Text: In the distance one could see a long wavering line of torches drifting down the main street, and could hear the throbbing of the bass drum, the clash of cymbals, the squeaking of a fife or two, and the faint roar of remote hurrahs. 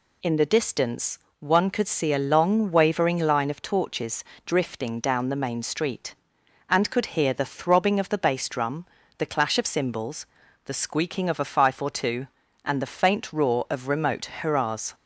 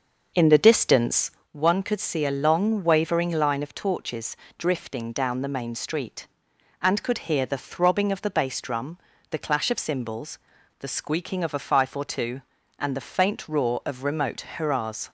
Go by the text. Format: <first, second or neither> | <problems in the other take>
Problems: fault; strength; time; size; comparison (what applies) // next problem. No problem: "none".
first | starts louder than the rest; noticeable; until 1.5 s; 6 dB // pauses between "distance" and "one"; slight; at 1.2 s; 0.22 s long; slight in the first // pauses between "torches" and "drifting"; slight; at 4.3 s; 0.22 s long; slight in the first